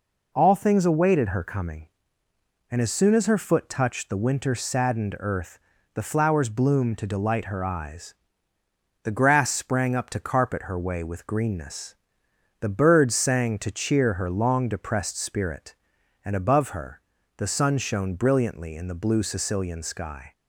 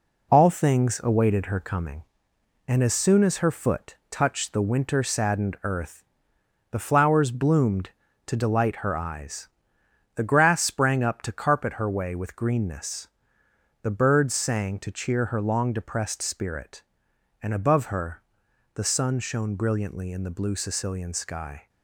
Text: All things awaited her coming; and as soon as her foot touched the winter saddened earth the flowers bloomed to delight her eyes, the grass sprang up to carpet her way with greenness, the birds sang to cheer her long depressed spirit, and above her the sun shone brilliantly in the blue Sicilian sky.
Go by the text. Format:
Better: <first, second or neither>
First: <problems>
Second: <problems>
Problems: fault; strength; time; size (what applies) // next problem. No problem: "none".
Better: first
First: pauses between "earth" and "the"; slight; at 5.5 s; 0.36 s long // pauses between "her" and "the"; slight; at 17.0 s; 0.34 s long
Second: gets quieter; noticeable; throughout; 6 dB // pauses between "earth" and "the"; noticeable; at 6.0 s; 0.66 s long // pauses between "her" and "the"; noticeable; at 18.2 s; 0.54 s long